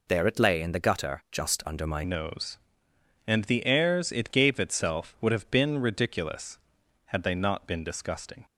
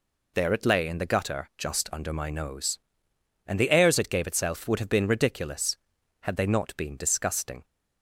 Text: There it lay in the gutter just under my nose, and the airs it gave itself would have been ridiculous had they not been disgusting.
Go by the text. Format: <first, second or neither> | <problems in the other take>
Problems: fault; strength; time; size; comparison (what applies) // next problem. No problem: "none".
second | changes voice at "nose"; from 2.0 s on; 6.4 s long